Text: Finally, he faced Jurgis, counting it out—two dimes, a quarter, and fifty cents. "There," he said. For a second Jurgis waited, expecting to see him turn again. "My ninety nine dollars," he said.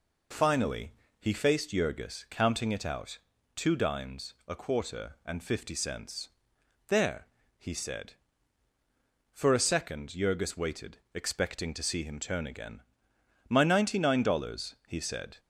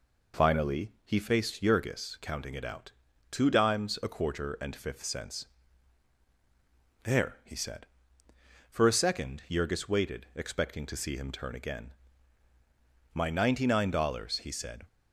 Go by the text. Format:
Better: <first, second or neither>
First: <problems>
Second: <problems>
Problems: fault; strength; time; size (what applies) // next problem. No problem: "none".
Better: first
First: none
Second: says "fifth" for "fifty"; at 4.7 s